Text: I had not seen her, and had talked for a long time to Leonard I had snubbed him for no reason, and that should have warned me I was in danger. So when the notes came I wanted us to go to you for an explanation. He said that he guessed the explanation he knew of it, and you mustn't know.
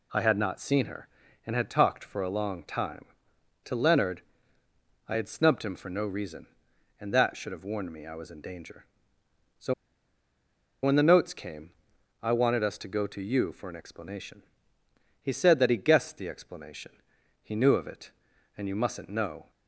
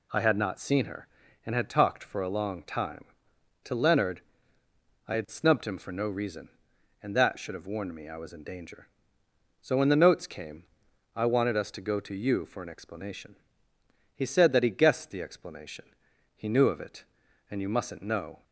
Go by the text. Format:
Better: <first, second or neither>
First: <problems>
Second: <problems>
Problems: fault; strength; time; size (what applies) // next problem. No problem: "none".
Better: second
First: pauses between "Leonard" and "I"; noticeable; at 4.2 s; 0.86 s long // pauses between "So" and "when"; at 9.7 s; 1.1 s long // pauses between "came" and "I"; noticeable; at 11.7 s; 0.50 s long // pauses between "explanation" and "he"; noticeable; at 16.9 s; 0.50 s long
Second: pauses between "Leonard" and "I"; noticeable; at 4.2 s; 0.86 s long // pauses between "came" and "I"; noticeable; at 10.6 s; 0.50 s long // pauses between "explanation" and "he"; noticeable; at 15.8 s; 0.50 s long